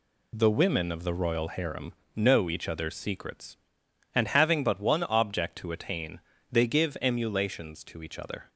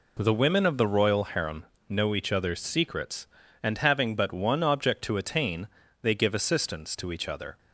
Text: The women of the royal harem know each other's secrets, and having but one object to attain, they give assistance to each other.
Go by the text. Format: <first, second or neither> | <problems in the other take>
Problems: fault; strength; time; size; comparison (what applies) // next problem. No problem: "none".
second | pauses between "harem" and "know"; slight; at 1.9 s; 0.24 s long; slight in the second // says "emulations" for "assistance"; at 7.0 s